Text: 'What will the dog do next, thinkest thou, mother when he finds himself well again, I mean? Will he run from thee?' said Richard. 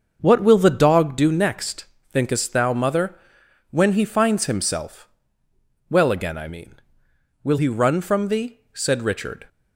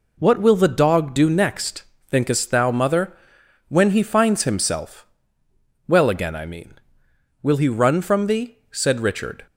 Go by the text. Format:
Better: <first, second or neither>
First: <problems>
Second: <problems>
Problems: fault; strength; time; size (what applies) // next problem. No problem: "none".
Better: second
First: starts louder than the rest; until 1.2 s; 6.5 dB // pauses between "mother" and "when"; noticeable; at 3.1 s; 0.58 s long // pauses between "himself" and "well"; noticeable; at 5.0 s; 0.80 s long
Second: pauses between "mother" and "when"; noticeable; at 3.1 s; 0.58 s long // pauses between "himself" and "well"; noticeable; at 5.0 s; 0.80 s long